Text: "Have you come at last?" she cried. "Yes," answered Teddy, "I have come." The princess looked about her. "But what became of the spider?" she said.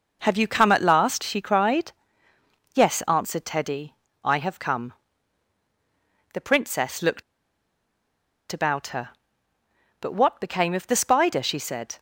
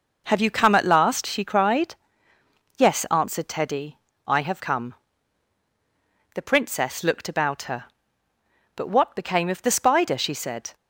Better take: second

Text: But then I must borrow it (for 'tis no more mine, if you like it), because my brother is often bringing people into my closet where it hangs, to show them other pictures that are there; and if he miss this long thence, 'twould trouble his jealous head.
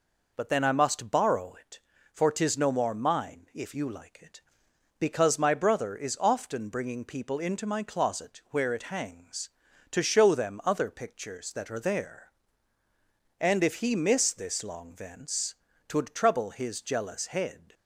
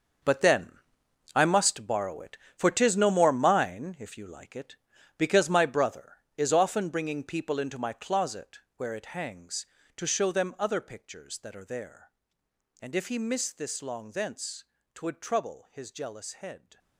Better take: first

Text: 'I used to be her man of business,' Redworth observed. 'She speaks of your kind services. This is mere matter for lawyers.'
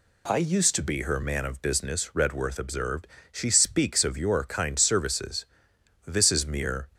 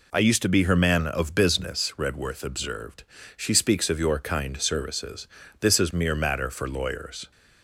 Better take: second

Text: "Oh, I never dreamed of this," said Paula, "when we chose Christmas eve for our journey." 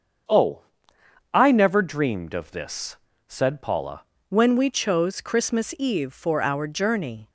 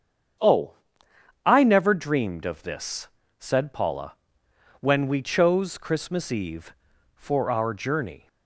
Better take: second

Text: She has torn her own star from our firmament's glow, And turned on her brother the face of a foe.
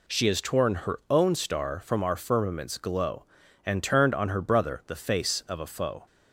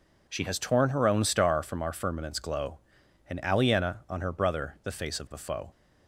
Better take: first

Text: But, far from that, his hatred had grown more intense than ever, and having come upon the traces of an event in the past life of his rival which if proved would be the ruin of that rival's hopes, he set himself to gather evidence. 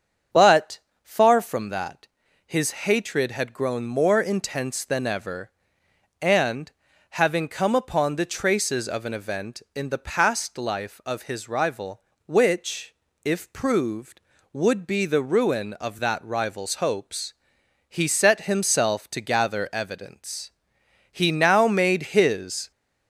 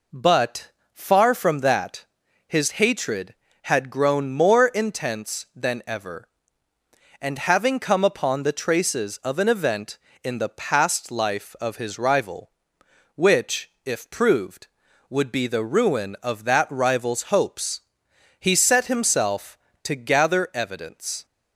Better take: second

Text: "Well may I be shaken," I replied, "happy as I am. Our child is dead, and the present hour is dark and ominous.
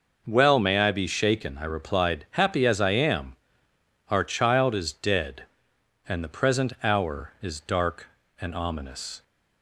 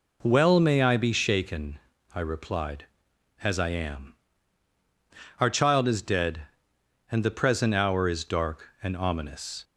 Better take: first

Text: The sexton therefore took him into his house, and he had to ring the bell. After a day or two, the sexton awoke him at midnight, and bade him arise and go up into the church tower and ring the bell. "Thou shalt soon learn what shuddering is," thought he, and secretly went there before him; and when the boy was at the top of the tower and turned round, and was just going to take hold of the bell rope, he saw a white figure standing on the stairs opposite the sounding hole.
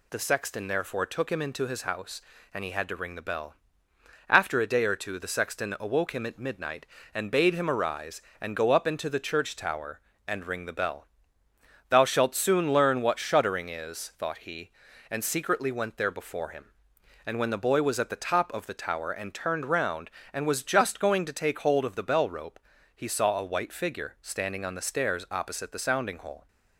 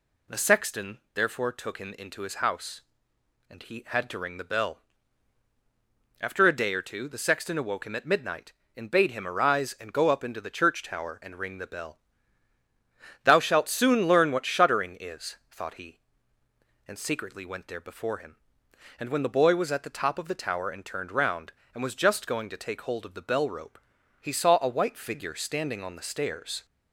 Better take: first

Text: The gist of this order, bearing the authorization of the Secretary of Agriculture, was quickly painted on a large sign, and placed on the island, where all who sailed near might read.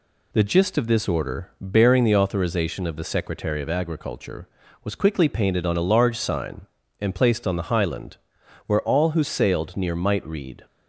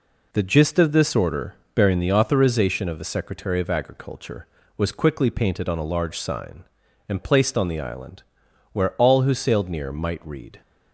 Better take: second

